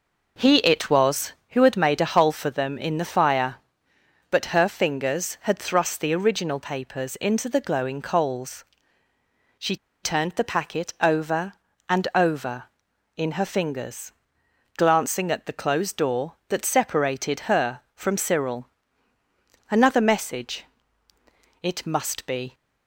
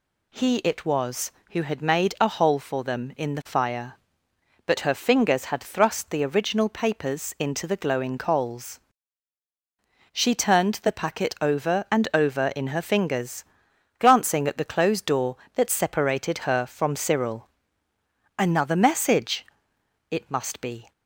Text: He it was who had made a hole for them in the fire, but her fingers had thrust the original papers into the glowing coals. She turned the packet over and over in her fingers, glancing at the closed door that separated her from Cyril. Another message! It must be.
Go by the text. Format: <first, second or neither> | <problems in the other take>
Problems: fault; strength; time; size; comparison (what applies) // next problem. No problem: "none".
second | pauses between "She" and "turned"; slight; at 9.7 s; 0.28 s long